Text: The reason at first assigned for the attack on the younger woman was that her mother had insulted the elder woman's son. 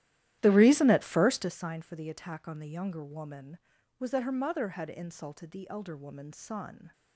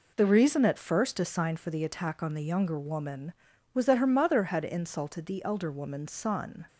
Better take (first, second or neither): second